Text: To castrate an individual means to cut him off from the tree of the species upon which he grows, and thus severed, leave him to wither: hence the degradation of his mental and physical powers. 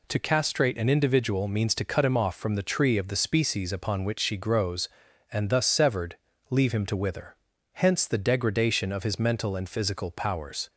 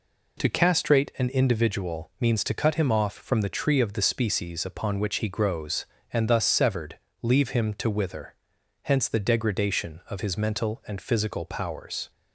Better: second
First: says "she" for "he"; at 4.1 s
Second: none

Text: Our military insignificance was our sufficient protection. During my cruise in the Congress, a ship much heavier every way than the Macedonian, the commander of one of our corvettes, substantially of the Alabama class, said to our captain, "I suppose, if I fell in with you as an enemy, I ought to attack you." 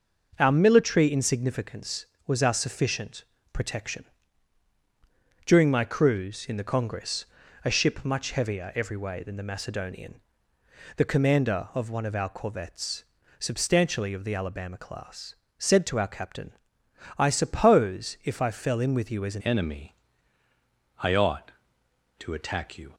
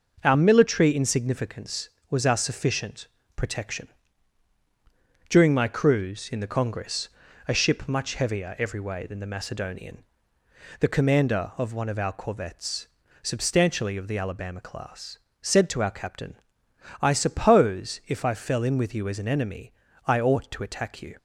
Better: second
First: pauses between "sufficient" and "protection"; slight; at 3.2 s; 0.28 s long // changes voice at "enemy"; from 19.4 s on; 3.5 s long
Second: pauses between "sufficient" and "protection"; slight; at 3.0 s; 0.28 s long

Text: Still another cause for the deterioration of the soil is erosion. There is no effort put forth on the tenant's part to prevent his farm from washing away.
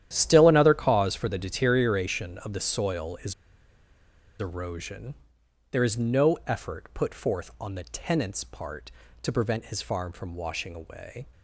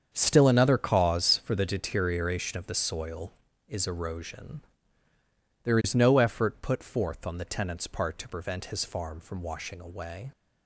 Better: second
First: starts louder than the rest; strong; until 1.1 s; 11 dB // pauses between "is" and "erosion"; at 3.3 s; 1.0 s long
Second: starts louder than the rest; strong; until 1.1 s; 7.5 dB

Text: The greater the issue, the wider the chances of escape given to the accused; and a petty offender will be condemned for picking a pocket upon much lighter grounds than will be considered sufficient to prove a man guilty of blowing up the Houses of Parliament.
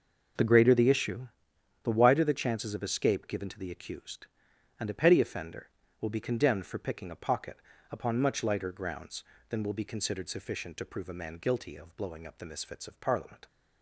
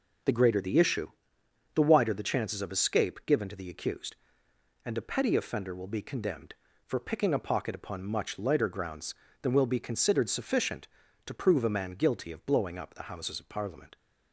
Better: second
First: pauses between "pocket" and "upon"; slight; at 7.5 s; 0.34 s long // says "Misfits" for "Houses"; at 12.4 s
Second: none

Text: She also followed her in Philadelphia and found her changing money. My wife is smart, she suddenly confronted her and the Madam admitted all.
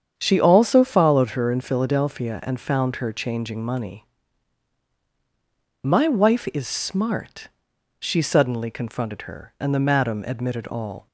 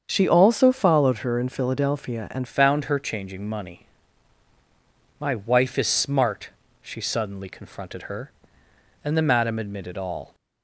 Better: first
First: starts louder than the rest; strong; until 1.1 s; 8 dB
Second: starts louder than the rest; strong; until 1.0 s; 7 dB // changes voice at "found"; from 2.4 s on; 7.9 s long

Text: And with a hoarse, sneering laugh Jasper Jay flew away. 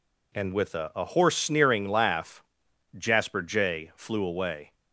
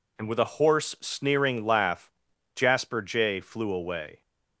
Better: second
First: says "a" twice; at 0.9 s // pauses between "laugh" and "Jasper"; noticeable; at 2.4 s; 0.56 s long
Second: pauses between "laugh" and "Jasper"; at 2.1 s; 0.44 s long

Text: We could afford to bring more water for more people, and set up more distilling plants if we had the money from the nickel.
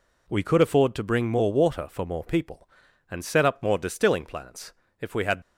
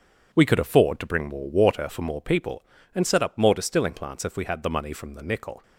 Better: second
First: pauses between "plants" and "if"; slight; at 4.7 s; 0.26 s long // stops before "the money from the nickel"; at 5.4 s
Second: none

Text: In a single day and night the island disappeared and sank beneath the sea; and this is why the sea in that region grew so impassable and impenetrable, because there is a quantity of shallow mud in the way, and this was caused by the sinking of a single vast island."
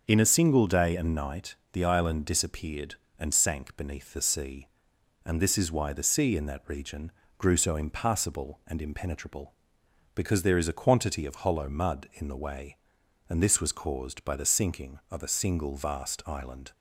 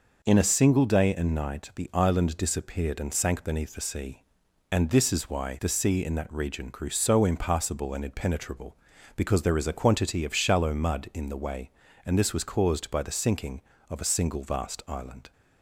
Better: second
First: starts louder than the rest; until 1.0 s; 6.5 dB // pauses between "night" and "the"; slight; at 1.5 s; 0.16 s long // pauses between "region" and "grew"; slight; at 7.0 s; 0.28 s long // says "hollow" for "shallow"; at 11.3 s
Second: none

